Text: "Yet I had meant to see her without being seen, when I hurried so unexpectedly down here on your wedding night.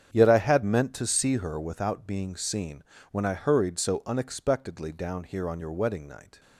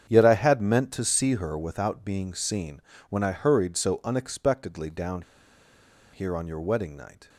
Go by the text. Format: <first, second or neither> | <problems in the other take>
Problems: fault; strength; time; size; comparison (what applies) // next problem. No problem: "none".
first | starts louder than the rest; strong; until 1.1 s; 8 dB; strong in the first // pauses between "down" and "here"; noticeable; at 5.2 s; 0.91 s long